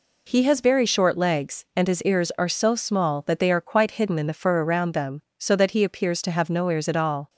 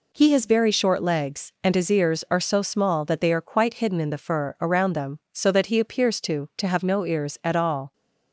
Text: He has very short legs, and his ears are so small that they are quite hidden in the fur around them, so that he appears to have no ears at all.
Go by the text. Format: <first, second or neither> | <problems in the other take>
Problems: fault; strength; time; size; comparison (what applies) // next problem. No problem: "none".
first | says "to" twice; at 6.5 s